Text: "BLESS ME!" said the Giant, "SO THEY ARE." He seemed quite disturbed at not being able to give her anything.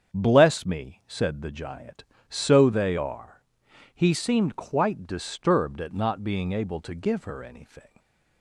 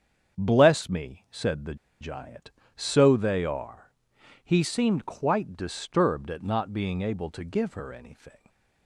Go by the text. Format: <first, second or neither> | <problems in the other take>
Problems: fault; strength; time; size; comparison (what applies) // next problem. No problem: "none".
first | starts louder than the rest; strong; until 1.4 s; 7.5 dB; strong in the first // pauses between "the" and "Giant"; slight; at 1.7 s; 0.25 s long // stays silent after the last word; slight; from 8.3 s on; 0.5 s long